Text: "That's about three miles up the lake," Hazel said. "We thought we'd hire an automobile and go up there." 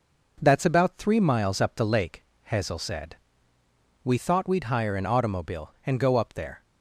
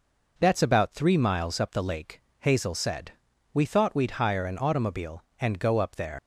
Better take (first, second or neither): first